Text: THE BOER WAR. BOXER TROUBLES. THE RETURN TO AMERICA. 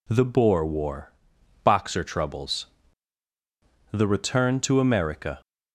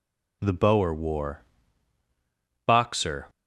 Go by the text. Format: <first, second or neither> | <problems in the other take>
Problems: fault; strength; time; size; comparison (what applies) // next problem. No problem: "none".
first | stops before "TROUBLES THE RETURN TO AMERICA"; at 3.2 s